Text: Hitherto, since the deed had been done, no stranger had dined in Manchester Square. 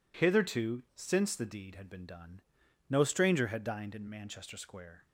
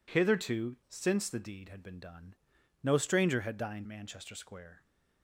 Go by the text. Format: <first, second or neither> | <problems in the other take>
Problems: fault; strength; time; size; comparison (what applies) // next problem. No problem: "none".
first | skips "in"; at 3.8 s